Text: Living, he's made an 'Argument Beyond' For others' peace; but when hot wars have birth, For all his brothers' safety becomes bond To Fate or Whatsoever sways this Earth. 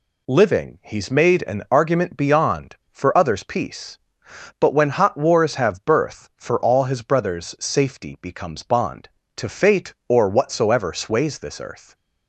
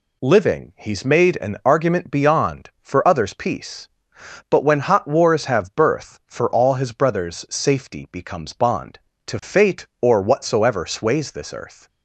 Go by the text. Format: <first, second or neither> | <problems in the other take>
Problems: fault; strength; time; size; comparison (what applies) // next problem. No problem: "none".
neither | none